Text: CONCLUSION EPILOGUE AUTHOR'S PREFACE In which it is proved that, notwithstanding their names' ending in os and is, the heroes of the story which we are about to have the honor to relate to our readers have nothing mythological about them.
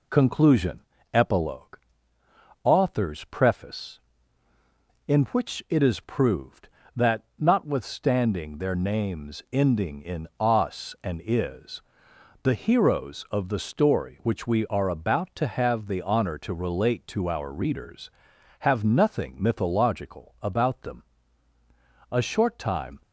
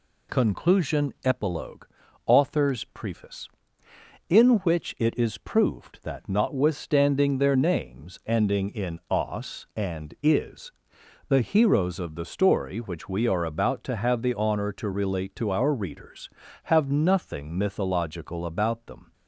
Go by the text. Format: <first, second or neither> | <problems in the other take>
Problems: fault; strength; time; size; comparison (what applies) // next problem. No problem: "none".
second | pauses between "CONCLUSION" and "EPILOGUE"; slight; at 0.8 s; 0.32 s long // pauses between "EPILOGUE" and "AUTHOR'S"; noticeable; at 1.7 s; 0.84 s long; also in the second // goes on to say "A short time"; noticeable; from 22.1 s on; 0.90 s long